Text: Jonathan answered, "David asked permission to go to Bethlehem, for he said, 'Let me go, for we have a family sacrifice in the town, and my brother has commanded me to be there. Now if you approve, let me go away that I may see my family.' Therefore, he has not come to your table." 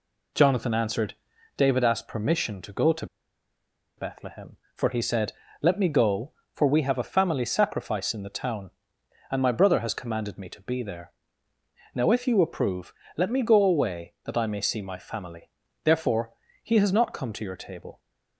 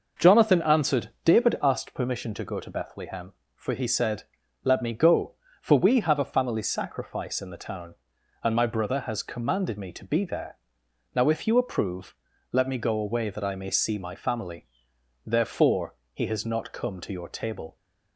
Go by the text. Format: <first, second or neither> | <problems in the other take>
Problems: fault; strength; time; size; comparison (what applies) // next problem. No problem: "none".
second | pauses between "to" and "Bethlehem"; noticeable; at 3.0 s; 0.92 s long